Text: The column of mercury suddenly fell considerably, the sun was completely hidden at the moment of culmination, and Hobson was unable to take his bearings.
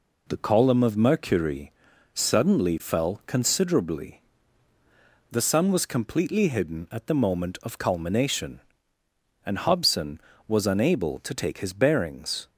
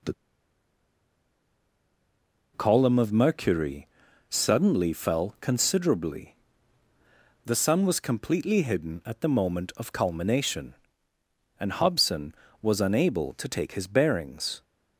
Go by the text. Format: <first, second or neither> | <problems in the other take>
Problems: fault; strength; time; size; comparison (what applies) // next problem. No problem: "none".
first | pauses between "The" and "column"; strong; at 0.1 s; 2.4 s long // pauses between "mercury" and "suddenly"; at 3.8 s; 0.42 s long; also in the first